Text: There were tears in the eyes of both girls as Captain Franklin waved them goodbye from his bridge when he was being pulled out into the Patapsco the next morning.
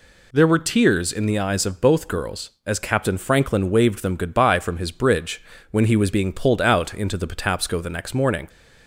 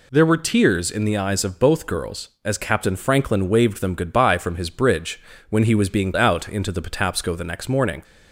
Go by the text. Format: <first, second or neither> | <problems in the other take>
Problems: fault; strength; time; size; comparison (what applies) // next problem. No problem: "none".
first | pauses between "bridge" and "when"; slight; at 5.1 s; 0.30 s long; slight in the first // skips "pulled"; at 6.1 s